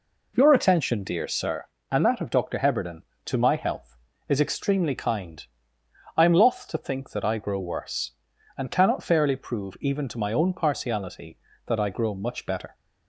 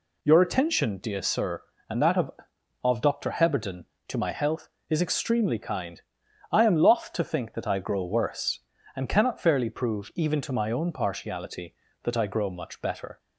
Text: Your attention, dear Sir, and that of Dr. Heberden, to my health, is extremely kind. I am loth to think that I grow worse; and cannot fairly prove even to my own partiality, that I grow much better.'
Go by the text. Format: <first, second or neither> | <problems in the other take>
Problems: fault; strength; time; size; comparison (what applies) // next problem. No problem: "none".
first | says "of" twice; at 2.8 s